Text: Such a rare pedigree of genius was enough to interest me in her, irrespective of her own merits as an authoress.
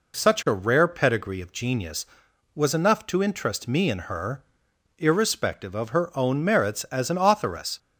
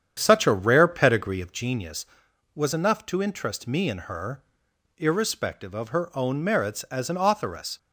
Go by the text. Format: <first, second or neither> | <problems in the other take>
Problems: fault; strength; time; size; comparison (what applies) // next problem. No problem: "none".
first | starts louder than the rest; strong; until 1.8 s; 8.5 dB